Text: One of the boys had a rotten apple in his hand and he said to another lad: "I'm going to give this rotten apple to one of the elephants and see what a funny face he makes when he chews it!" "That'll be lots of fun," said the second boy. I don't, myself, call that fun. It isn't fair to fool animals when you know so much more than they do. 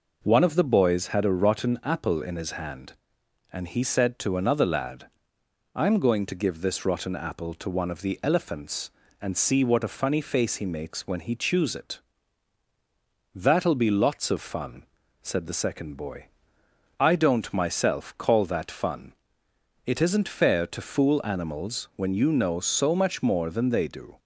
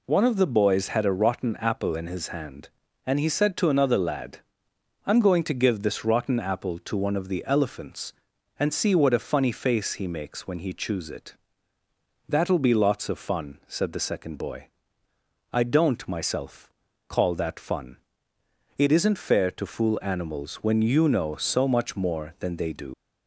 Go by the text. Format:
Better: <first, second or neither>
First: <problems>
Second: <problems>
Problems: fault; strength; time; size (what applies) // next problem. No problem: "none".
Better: first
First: none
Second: leaves "do" unfinished; at 22.9 s; 80 ms